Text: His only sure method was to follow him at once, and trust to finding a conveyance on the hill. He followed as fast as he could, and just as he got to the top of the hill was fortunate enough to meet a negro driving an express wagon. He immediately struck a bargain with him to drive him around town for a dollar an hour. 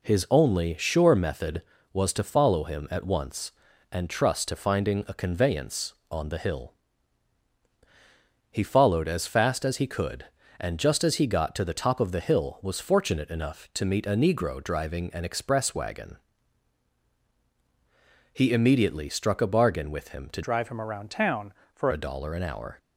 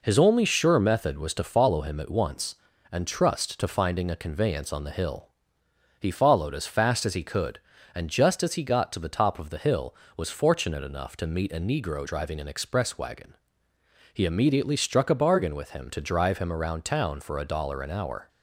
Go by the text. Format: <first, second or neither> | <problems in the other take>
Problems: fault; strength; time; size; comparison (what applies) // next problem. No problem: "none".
second | changes voice from "drive" to "for"; from 20.4 to 21.9 s; 1.5 s long